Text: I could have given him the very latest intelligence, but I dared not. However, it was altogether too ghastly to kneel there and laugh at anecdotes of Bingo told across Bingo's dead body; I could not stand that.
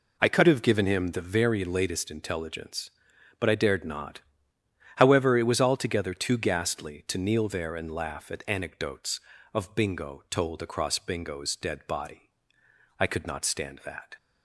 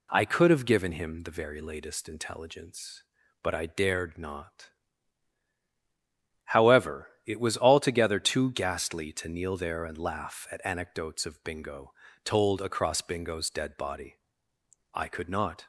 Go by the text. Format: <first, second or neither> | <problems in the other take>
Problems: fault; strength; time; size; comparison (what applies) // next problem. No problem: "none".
first | pauses between "Bingo" and "told"; slight; at 11.9 s; 0.30 s long // stops before "stand that"; at 15.6 s